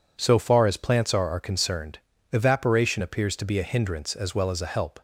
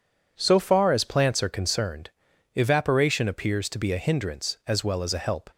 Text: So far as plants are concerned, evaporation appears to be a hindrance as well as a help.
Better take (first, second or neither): second